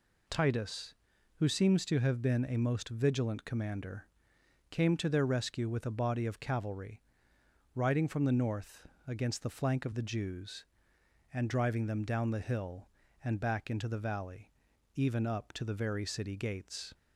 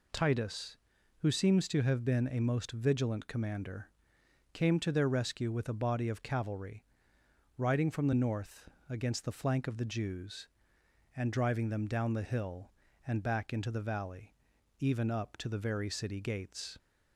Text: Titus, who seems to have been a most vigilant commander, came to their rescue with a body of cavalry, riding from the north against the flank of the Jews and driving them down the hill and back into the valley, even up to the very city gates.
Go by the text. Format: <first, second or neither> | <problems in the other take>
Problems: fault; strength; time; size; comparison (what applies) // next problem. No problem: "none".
neither | pauses between "north" and "against"; slight; the same in both